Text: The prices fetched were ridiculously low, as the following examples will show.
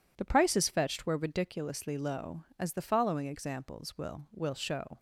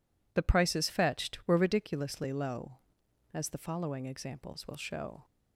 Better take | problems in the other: second | says "will" twice; at 4.3 s

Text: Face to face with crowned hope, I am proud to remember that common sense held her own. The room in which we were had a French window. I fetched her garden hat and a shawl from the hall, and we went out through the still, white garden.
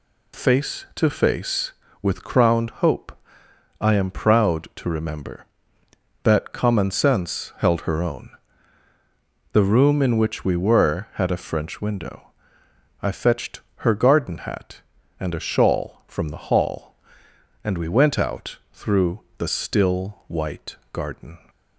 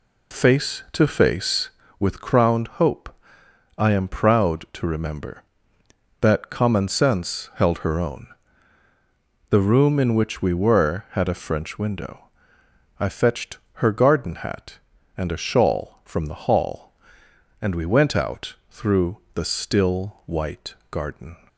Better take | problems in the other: first | starts louder than the rest; slight; until 1.9 s; 2.5 dB // pauses between "crowned" and "hope"; slight; at 2.6 s; 0.16 s long; slight in the first // pauses between "fetched" and "her"; slight; at 13.5 s; 0.16 s long; slight in the first // pauses between "through" and "the"; slight; at 19.1 s; 0.17 s long; slight in the first // pauses between "white" and "garden"; slight; at 20.7 s; 0.16 s long; slight in the first

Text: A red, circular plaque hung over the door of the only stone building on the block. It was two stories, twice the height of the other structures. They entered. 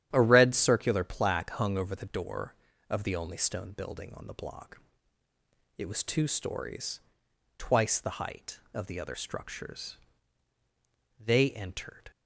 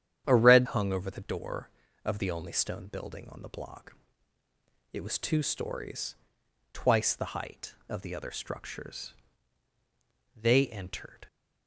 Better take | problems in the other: first | starts louder than the rest; strong; until 1.2 s; 9.5 dB; strong in the first // skips "circular plaque"; at 0.6 s

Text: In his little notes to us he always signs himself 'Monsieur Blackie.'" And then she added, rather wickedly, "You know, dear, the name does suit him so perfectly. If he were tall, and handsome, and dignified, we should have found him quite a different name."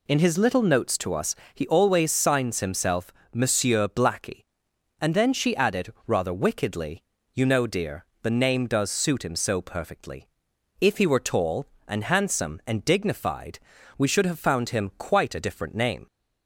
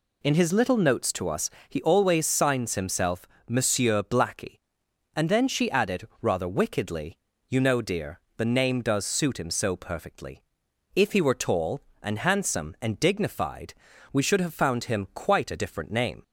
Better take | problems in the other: neither | pauses between "us" and "he"; slight; the same in both // pauses between "himself" and "Monsieur"; slight; the same in both

